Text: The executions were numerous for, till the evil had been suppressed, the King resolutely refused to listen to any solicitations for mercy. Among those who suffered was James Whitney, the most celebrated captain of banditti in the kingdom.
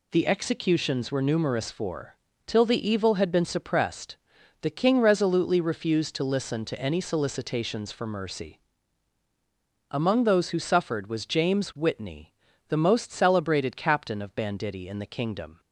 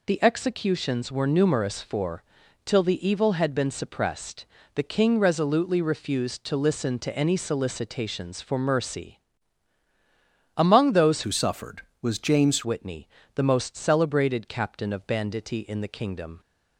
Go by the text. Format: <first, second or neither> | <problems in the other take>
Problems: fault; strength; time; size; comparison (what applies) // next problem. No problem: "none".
first | changes voice from "who" to "James"; from 11.2 to 12.6 s; 1.4 s long